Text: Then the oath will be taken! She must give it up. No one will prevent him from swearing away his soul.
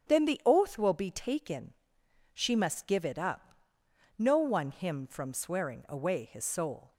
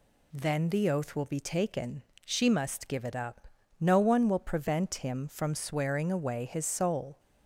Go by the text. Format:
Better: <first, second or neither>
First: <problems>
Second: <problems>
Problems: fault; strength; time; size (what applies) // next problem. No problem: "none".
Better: second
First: starts louder than the rest; strong; until 1.1 s; 8 dB // skips "will prevent"; at 4.7 s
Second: none